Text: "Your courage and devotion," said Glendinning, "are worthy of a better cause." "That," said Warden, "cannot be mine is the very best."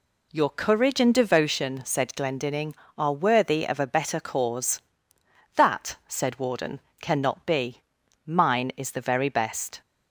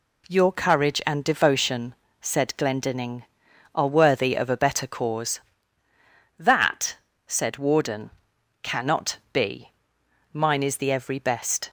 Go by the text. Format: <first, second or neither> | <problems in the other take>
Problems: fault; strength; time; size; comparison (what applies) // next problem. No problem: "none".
first | pauses between "be" and "mine"; noticeable; at 9.7 s; 0.60 s long; noticeable in the first // says "every" for "very"; at 10.9 s